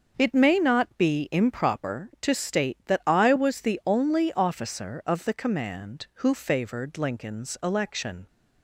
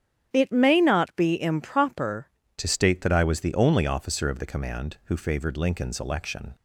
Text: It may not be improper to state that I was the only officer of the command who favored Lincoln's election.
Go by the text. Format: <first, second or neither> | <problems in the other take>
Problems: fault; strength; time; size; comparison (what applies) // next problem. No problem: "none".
first | starts louder than the rest; strong; until 1.3 s; 9.5 dB; also in the first // changes voice at "to"; from 2.5 s on; 4.0 s long